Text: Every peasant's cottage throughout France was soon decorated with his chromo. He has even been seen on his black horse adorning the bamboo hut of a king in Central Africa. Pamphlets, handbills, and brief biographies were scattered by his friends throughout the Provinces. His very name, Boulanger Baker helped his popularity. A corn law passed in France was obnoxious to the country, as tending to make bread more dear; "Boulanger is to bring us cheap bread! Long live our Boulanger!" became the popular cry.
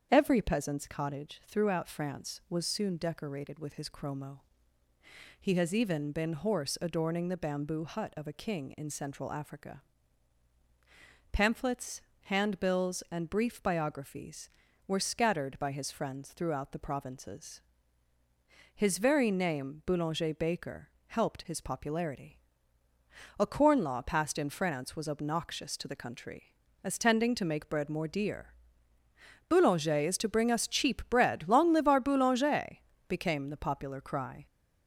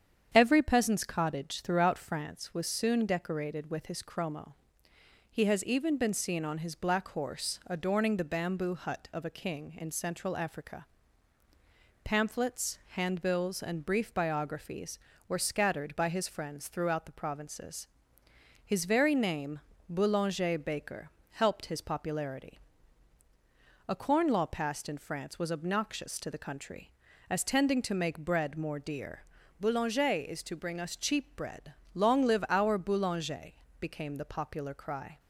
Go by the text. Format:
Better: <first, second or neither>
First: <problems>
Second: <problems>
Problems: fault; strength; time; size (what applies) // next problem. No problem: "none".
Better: second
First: starts louder than the rest; strong; until 1.1 s; 8 dB // skips "seen on his black"; at 6.3 s // pauses between "Baker" and "helped"; slight; at 20.8 s; 0.18 s long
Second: starts louder than the rest; strong; until 1.3 s; 8 dB // pauses between "Baker" and "helped"; slight; at 21.0 s; 0.22 s long